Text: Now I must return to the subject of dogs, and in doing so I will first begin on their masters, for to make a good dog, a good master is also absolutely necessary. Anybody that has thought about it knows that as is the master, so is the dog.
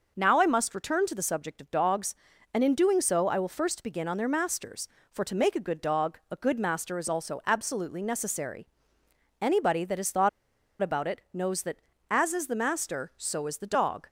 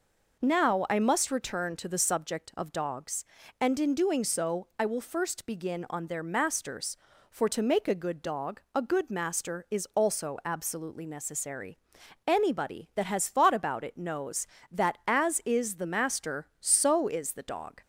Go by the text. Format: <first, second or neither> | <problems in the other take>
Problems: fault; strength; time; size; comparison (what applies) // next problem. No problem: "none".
second | pauses between "thought" and "about"; noticeable; at 10.2 s; 0.52 s long